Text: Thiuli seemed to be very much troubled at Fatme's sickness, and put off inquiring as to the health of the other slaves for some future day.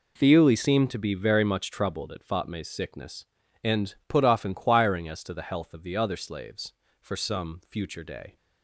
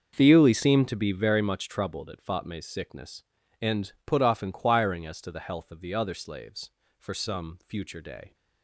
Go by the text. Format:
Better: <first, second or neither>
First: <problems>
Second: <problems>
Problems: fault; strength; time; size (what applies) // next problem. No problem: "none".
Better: first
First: none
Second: starts louder than the rest; until 1.3 s; 6.5 dB